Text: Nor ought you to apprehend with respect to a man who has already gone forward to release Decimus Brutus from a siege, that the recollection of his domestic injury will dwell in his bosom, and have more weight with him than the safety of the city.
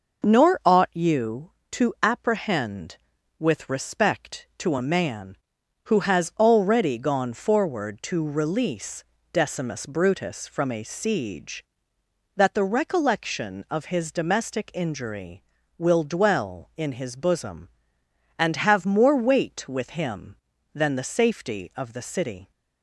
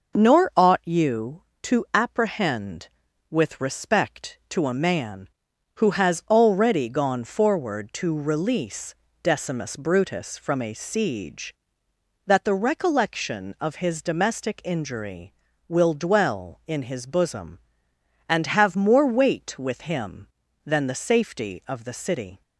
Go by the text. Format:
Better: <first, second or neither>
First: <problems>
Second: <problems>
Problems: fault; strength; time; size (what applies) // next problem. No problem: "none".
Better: neither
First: pauses between "release" and "Decimus"; slight; at 9.0 s; 0.28 s long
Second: pauses between "release" and "Decimus"; slight; at 8.9 s; 0.27 s long